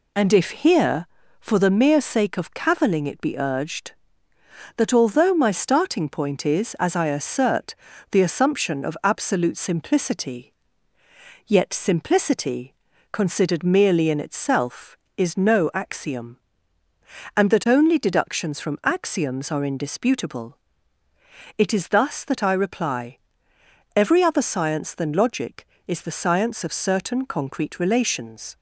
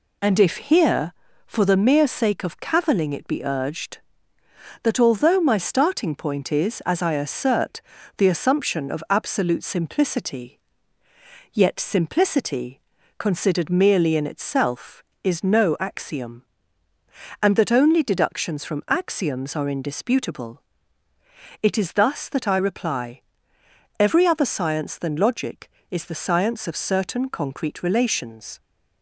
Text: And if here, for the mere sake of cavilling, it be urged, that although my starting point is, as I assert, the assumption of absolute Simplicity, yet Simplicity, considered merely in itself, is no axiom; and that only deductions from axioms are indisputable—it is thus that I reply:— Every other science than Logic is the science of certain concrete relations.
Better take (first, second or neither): neither